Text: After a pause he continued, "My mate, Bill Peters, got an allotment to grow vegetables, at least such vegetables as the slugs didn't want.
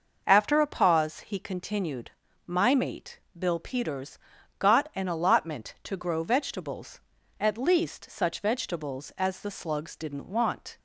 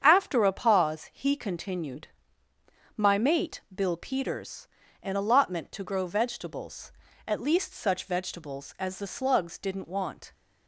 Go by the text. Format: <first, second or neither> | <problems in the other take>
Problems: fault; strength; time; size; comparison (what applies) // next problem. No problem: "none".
first | starts louder than the rest; strong; until 1.0 s; 8 dB // skips "got"; at 4.8 s